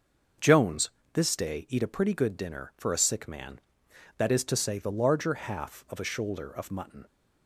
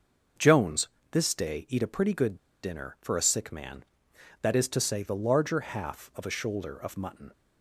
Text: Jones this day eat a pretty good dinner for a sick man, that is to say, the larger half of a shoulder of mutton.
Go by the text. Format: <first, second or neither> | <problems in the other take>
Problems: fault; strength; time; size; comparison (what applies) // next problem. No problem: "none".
first | starts louder than the rest; until 1.6 s; 6.5 dB; also in the first // pauses between "Jones" and "this"; slight; at 0.8 s; 0.24 s long; slight in the first // pauses between "good" and "dinner"; slight; at 2.3 s; 0.25 s long